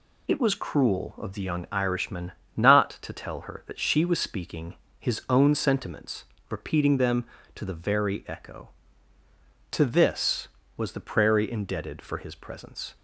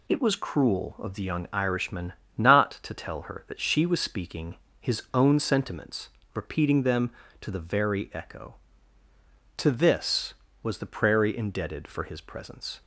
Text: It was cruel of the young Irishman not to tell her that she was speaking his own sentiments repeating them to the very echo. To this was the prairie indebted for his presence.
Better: neither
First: pauses between "Irishman" and "not"; slight; at 2.3 s; 0.24 s long // pauses between "speaking" and "his"; slight; at 4.7 s; 0.24 s long // pauses between "sentiments" and "repeating"; slight; at 6.2 s; 0.26 s long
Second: pauses between "Irishman" and "not"; slight; at 2.1 s; 0.24 s long // pauses between "speaking" and "his"; slight; at 4.5 s; 0.24 s long // pauses between "sentiments" and "repeating"; slight; at 6.0 s; 0.26 s long

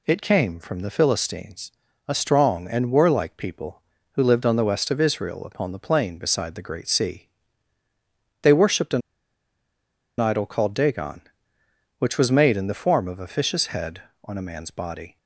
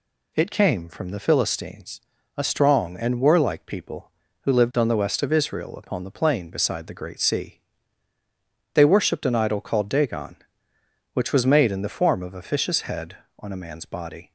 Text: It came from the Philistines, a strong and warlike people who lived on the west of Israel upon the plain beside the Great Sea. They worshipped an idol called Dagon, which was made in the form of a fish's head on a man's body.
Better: second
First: pauses between "an" and "idol"; at 9.0 s; 1.1 s long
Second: none

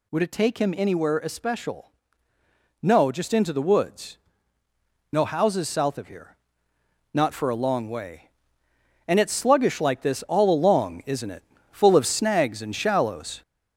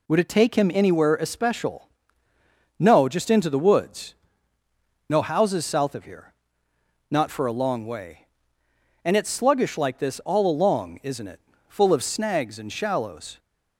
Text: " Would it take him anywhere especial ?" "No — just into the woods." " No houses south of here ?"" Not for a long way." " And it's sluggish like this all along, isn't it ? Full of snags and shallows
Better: second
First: gets louder; strong; throughout; 10 dB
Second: none

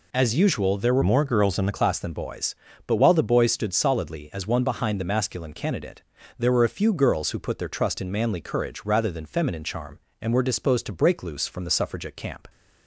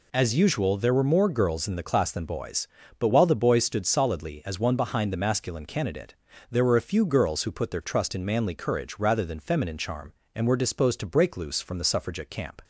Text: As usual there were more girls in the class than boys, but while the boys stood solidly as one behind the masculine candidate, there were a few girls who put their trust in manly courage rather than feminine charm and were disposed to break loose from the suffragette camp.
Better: second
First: changes voice from "more" to "the"; from 1.0 to 1.7 s; 0.7 s long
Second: none

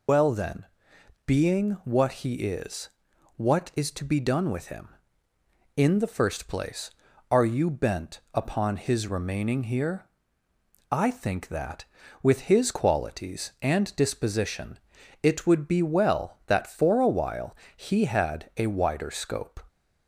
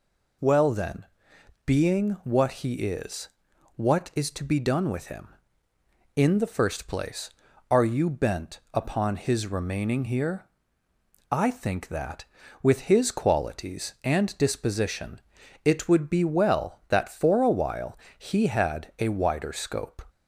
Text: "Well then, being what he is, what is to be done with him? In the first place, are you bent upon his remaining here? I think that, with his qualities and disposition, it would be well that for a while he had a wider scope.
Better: second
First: loses the start of "Well"; at 0.0 s; 75 ms // pauses between "while" and "he"; slight; at 17.5 s; 0.20 s long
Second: pauses between "while" and "he"; slight; at 17.9 s; 0.20 s long

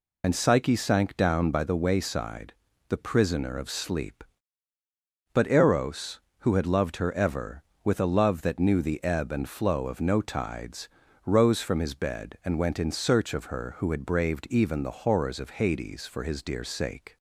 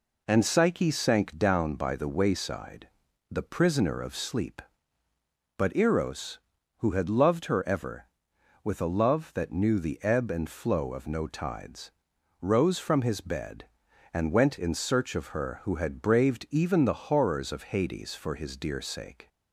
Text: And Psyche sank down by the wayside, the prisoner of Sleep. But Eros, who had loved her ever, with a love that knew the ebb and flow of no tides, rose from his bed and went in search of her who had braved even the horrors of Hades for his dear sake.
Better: second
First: loses the start of "And"; at 0.2 s; 55 ms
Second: none

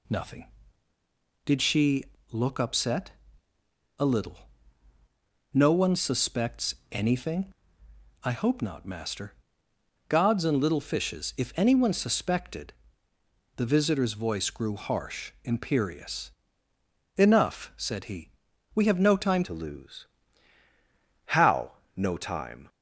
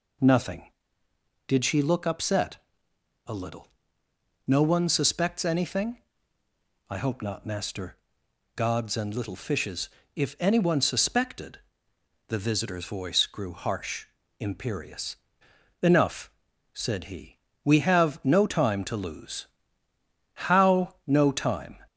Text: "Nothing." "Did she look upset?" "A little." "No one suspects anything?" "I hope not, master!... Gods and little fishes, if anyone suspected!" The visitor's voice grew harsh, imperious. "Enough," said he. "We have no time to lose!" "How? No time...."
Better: second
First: pauses between "she" and "look"; slight; at 2.0 s; 0.26 s long // pauses between "suspects" and "anything"; slight; at 6.7 s; 0.18 s long // changes voice at "to"; from 19.4 s on; 3.2 s long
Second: none

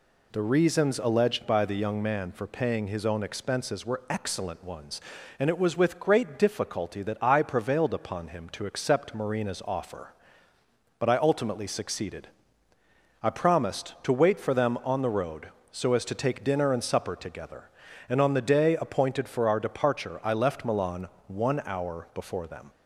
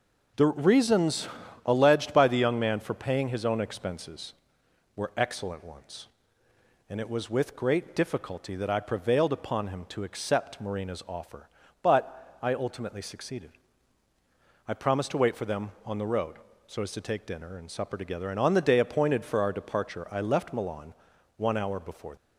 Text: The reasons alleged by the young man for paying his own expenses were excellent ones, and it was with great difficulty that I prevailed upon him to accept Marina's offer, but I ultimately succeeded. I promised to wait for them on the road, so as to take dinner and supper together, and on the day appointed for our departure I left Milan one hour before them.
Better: first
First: pauses between "Milan" and "one"; slight; at 21.0 s; 0.18 s long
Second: pauses between "reasons" and "alleged"; slight; at 1.2 s; 0.36 s long // pauses between "Milan" and "one"; at 20.9 s; 0.44 s long // stops before "them"; at 22.1 s

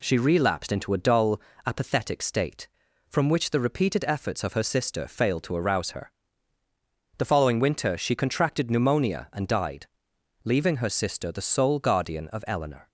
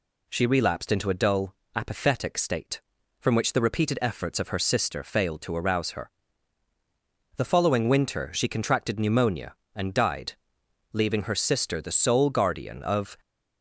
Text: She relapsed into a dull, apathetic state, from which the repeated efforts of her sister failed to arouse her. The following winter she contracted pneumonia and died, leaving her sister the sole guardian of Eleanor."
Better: first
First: none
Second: stops before "Eleanor"; at 13.1 s

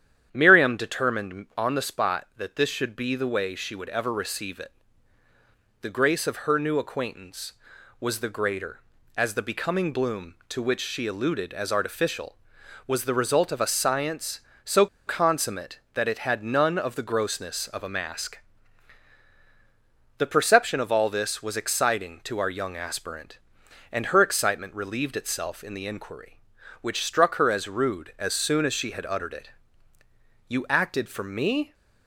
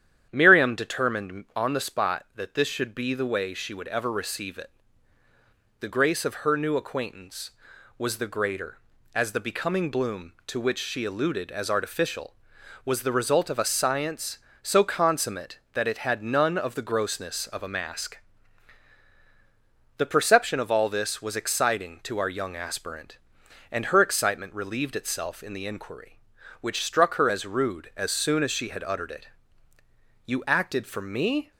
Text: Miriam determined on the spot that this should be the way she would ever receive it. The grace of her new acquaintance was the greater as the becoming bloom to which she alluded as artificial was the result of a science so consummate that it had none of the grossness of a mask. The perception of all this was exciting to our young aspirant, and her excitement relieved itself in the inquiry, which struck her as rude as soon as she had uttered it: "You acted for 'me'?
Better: second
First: starts louder than the rest; strong; until 1.3 s; 10 dB // pauses between "so" and "consummate"; slight; at 14.8 s; 0.21 s long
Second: starts louder than the rest; strong; until 1.3 s; 10 dB

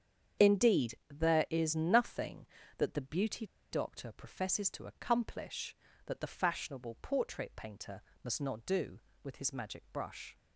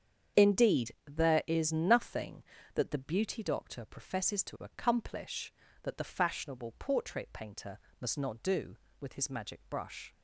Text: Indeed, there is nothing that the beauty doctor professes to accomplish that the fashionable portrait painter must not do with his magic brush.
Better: second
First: starts louder than the rest; strong; until 1.5 s; 8 dB // pauses between "beauty" and "doctor"; slight; at 3.4 s; 0.26 s long // pauses between "painter" and "must"; slight; at 7.9 s; 0.22 s long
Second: starts louder than the rest; strong; until 1.5 s; 8 dB // pauses between "painter" and "must"; slight; at 7.7 s; 0.22 s long

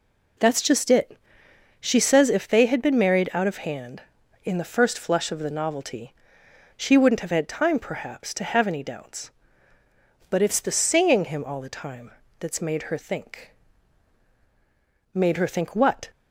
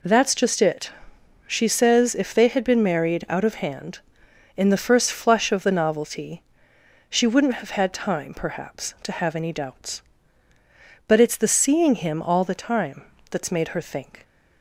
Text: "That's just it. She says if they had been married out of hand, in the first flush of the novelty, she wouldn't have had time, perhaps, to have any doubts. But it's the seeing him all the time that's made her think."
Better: second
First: pauses between "time" and "that's"; slight; at 12.1 s; 0.28 s long // goes on to say "Made her think what"; noticeable; from 15.1 s on; 0.98 s long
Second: pauses between "time" and "that's"; slight; at 13.0 s; 0.24 s long

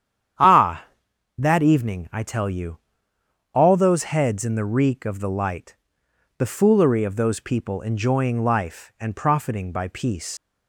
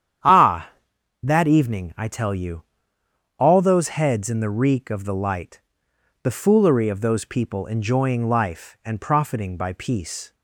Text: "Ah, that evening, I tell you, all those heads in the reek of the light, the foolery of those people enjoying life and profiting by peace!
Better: second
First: starts louder than the rest; strong; until 1.9 s; 9.5 dB // leaves "peace" unfinished; at 10.3 s; 125 ms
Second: starts louder than the rest; strong; until 1.7 s; 9.5 dB

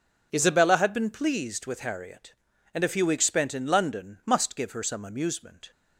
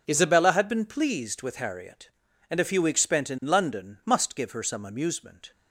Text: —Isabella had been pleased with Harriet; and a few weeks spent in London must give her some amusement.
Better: neither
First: none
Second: none

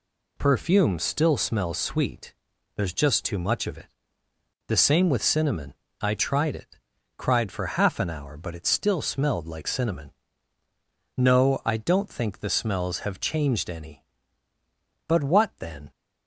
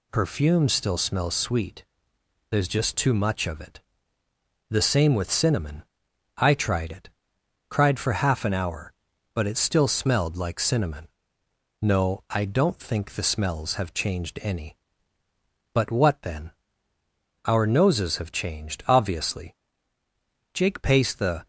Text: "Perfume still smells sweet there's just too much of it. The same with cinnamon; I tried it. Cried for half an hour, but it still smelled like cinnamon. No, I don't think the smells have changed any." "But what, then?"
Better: first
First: pauses between "sweet" and "there's"; at 2.3 s; 0.40 s long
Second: pauses between "sweet" and "there's"; noticeable; at 1.8 s; 0.66 s long // goes on to say "Our noses have changed obviously Jake paced the"; strong; from 17.4 s on; 4.0 s long

